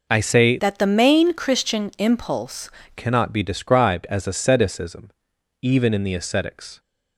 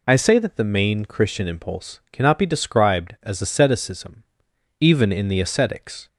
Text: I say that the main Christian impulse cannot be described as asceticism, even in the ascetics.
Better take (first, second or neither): second